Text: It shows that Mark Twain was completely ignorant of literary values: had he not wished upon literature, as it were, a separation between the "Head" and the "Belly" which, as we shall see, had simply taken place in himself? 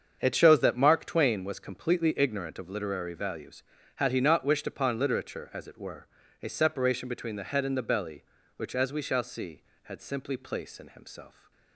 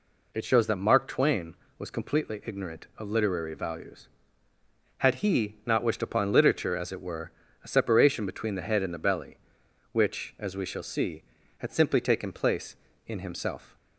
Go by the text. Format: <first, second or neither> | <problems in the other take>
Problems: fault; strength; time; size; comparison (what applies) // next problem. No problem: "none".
second | starts louder than the rest; until 1.2 s; 7 dB // skips "taken"; at 10.3 s